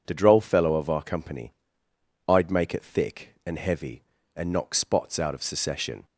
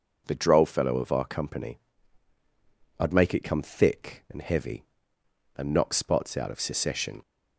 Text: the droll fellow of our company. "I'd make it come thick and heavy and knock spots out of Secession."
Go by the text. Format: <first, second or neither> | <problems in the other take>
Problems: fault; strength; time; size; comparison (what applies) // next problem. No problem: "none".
second | skips "come"; at 2.8 s